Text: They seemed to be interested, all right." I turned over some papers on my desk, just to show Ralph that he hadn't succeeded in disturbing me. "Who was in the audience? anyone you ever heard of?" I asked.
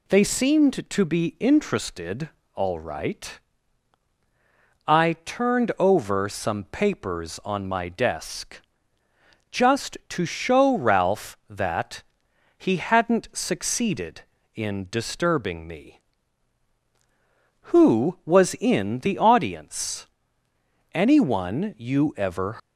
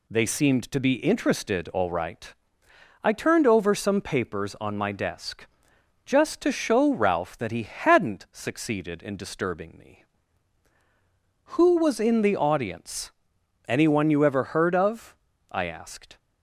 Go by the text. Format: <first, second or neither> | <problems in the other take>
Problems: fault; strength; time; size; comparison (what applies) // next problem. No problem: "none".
second | pauses between "that" and "he"; noticeable; at 12.0 s; 0.52 s long // stops before "heard of I asked"; at 22.5 s